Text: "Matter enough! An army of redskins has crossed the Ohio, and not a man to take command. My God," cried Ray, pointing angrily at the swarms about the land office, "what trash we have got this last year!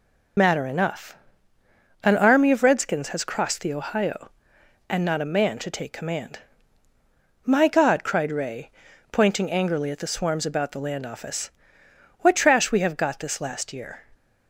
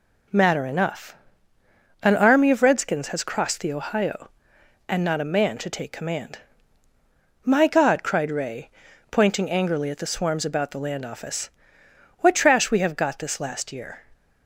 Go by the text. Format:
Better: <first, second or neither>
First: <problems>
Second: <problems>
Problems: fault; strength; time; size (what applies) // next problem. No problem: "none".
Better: second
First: loses the start of "Matter"; at 0.3 s; 65 ms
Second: none